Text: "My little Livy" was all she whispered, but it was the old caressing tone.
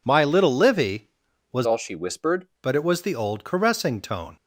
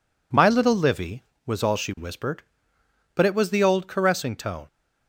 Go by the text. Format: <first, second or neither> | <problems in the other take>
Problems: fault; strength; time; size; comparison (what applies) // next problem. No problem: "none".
second | changes voice from "all" to "whispered"; from 1.6 to 2.4 s; 0.8 s long